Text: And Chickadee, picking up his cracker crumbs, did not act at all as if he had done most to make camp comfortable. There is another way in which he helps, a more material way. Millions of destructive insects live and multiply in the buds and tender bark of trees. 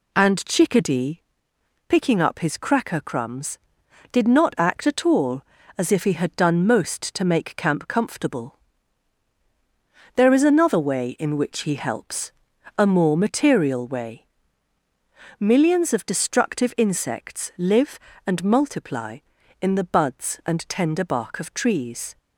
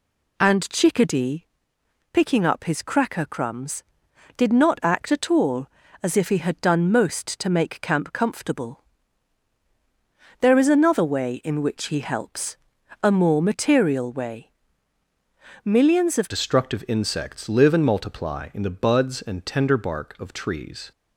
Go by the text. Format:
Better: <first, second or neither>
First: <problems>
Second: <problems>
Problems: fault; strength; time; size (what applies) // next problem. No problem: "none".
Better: first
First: none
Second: changes voice at "destructive"; from 16.2 s on; 4.7 s long